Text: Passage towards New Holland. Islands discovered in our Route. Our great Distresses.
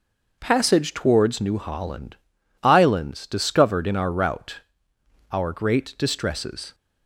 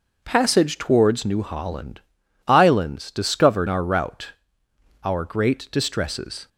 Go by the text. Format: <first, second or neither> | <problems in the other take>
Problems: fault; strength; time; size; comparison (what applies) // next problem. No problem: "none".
first | skips "in"; at 3.6 s